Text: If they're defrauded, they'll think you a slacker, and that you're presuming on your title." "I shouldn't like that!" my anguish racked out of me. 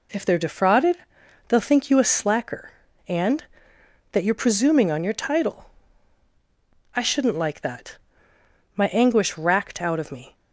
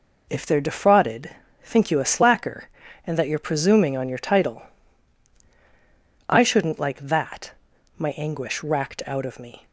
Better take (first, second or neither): first